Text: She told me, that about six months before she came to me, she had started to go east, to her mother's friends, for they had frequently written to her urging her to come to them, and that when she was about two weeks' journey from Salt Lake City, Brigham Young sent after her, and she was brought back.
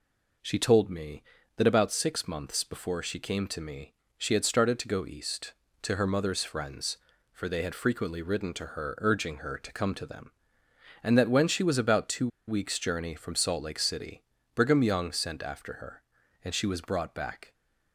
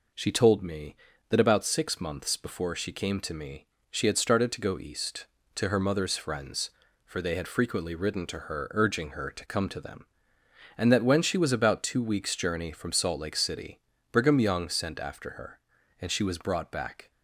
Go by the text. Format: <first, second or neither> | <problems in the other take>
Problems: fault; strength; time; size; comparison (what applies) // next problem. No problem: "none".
second | pauses between "two" and "weeks"; slight; at 12.2 s; 0.19 s long